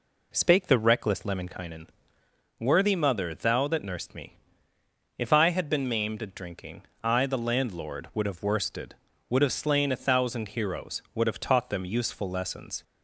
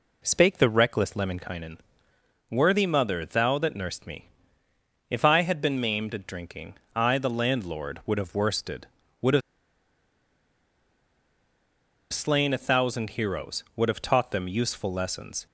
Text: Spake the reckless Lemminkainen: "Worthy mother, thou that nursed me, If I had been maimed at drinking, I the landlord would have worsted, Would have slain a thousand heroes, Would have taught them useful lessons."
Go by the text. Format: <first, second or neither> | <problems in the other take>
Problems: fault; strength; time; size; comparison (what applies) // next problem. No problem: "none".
first | pauses between "have" and "slain"; strong; at 9.4 s; 2.7 s long